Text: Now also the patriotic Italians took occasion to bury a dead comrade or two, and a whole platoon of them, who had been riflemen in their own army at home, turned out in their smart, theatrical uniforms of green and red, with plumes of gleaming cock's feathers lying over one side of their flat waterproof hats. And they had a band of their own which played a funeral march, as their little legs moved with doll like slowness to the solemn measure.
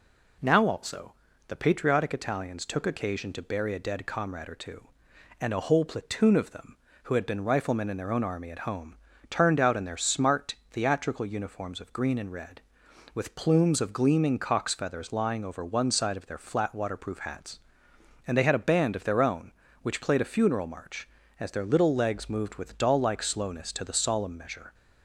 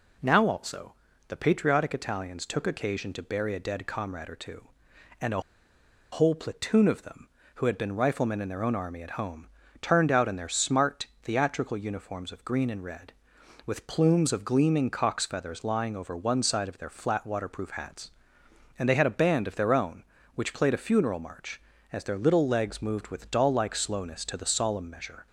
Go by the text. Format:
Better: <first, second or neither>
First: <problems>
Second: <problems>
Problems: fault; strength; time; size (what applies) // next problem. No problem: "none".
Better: first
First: pauses between "also" and "the"; slight; at 1.1 s; 0.36 s long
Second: pauses between "also" and "the"; slight; at 0.9 s; 0.36 s long // pauses between "a" and "whole"; noticeable; at 5.4 s; 0.71 s long